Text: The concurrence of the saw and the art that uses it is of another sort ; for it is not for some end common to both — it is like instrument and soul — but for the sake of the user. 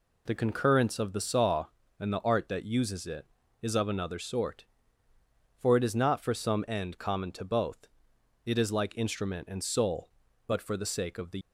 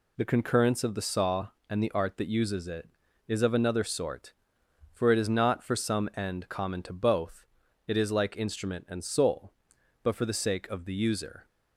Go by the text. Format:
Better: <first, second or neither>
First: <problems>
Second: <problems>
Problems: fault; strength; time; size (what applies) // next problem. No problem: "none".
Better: second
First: stops before "user"; at 11.4 s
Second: none